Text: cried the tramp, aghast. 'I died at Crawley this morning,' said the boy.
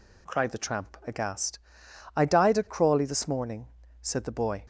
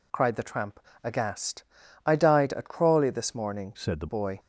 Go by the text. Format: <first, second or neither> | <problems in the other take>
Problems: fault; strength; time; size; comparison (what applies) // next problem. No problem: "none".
first | changes voice from "said" to "the"; from 3.7 to 4.0 s; 0.3 s long